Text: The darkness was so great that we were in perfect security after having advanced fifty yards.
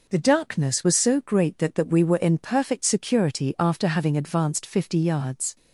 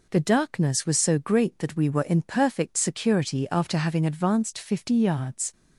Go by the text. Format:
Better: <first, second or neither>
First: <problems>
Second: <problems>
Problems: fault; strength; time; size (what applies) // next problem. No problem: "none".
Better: second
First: says "that" twice; at 1.7 s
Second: none